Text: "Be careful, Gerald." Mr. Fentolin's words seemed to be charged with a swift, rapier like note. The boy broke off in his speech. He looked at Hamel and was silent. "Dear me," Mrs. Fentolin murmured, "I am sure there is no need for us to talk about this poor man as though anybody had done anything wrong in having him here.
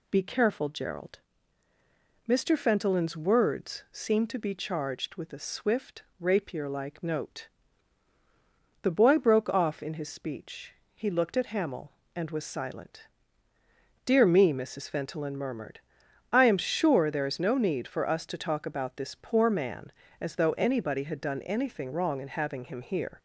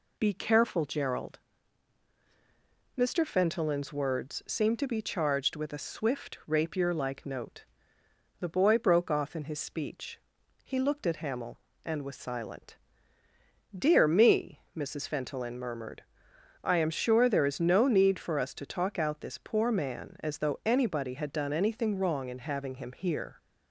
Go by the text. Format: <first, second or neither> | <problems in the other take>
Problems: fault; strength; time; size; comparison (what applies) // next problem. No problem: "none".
first | says "out" for "about"; at 18.9 s